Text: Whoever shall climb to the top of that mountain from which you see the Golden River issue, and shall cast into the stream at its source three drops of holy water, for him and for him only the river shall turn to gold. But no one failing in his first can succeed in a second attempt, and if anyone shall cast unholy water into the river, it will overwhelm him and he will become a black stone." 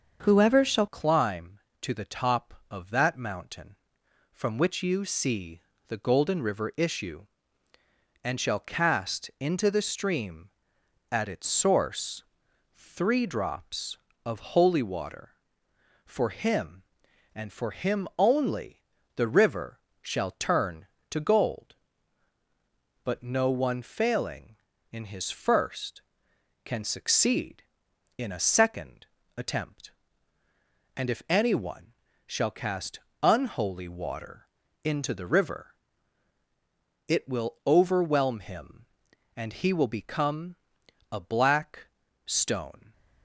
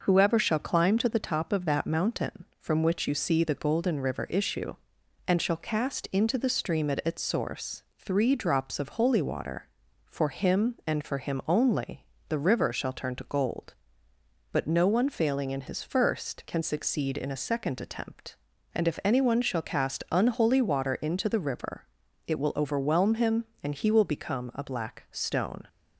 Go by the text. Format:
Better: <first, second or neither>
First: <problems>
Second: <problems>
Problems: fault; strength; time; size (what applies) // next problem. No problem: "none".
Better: second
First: starts louder than the rest; until 1.2 s; 6.5 dB // changes voice at "climb"; from 0.8 s on; 42.1 s long // pauses between "see" and "the"; slight; at 5.6 s; 0.28 s long // pauses between "source" and "three"; noticeable; at 12.2 s; 0.50 s long // pauses between "only" and "the"; slight; at 18.8 s; 0.36 s long // pauses between "river" and "shall"; slight; at 19.8 s; 0.20 s long // pauses between "second" and "attempt"; slight; at 29.0 s; 0.32 s long // pauses between "anyone" and "shall"; slight; at 31.9 s; 0.34 s long // pauses between "cast" and "unholy"; slight; at 32.9 s; 0.24 s long // pauses between "water" and "into"; at 34.4 s; 0.40 s long // pauses between "become" and "a"; noticeable; at 40.5 s; 0.54 s long // pauses between "black" and "stone"; at 41.8 s; 0.40 s long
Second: pauses between "source" and "three"; slight; at 7.8 s; 0.16 s long // pauses between "only" and "the"; slight; at 12.0 s; 0.26 s long